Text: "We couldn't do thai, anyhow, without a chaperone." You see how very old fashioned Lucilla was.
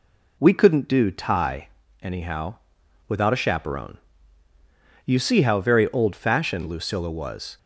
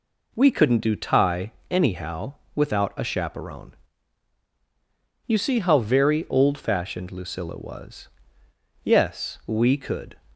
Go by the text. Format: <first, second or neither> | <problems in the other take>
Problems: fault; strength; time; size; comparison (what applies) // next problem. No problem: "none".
first | goes on to say "Yes we could"; from 8.8 s on; 1.3 s long